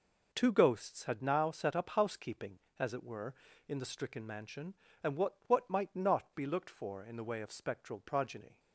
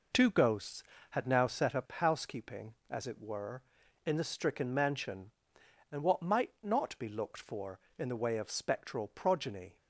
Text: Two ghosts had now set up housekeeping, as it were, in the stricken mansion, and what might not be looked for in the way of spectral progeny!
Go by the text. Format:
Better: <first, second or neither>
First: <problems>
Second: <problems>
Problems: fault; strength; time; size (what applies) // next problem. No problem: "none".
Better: second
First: says "what" twice; at 5.4 s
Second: none